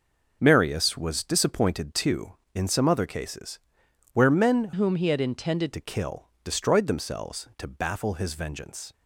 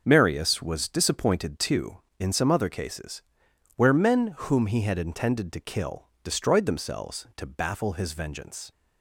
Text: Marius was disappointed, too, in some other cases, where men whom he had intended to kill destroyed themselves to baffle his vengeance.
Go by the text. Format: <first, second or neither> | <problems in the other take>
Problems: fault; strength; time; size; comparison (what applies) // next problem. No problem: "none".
second | changes voice from "whom" to "intended"; from 4.7 to 5.7 s; 1.0 s long